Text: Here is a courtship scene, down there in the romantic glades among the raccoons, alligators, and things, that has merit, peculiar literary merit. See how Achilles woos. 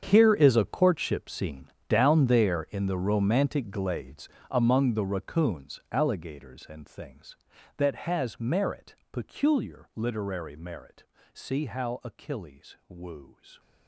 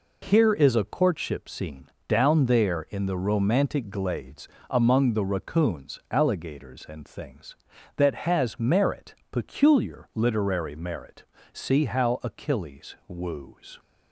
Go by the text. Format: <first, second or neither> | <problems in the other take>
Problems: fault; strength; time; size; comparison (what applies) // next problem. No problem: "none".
second | gets quieter; strong; throughout; 15.5 dB // pauses between "glades" and "among"; slight; at 4.2 s; 0.22 s long; slight in the second